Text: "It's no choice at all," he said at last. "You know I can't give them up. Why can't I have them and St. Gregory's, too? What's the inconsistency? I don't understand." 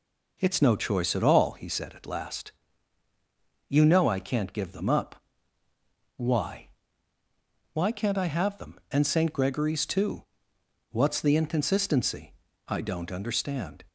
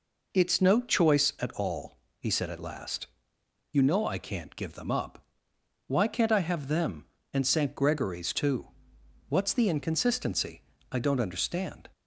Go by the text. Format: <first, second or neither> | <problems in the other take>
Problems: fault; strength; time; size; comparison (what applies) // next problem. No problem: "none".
second | says "Why" twice; at 7.7 s